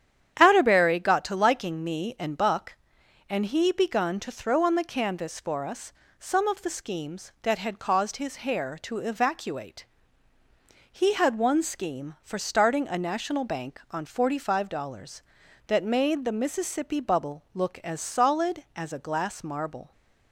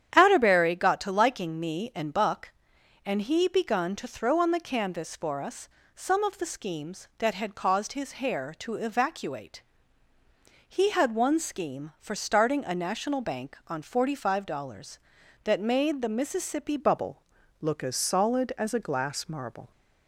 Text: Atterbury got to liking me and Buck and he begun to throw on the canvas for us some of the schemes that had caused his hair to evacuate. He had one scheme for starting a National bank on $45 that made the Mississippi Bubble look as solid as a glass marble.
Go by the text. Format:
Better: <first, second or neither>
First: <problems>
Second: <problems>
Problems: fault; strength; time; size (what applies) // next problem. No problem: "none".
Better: first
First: starts louder than the rest; strong; until 1.4 s; 9 dB // pauses between "us" and "some"; slight; at 5.9 s; 0.28 s long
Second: starts louder than the rest; strong; until 1.1 s; 9 dB // pauses between "us" and "some"; slight; at 5.6 s; 0.28 s long // changes voice at "Bubble"; from 16.7 s on; 3.0 s long // pauses between "Bubble" and "look"; at 17.2 s; 0.40 s long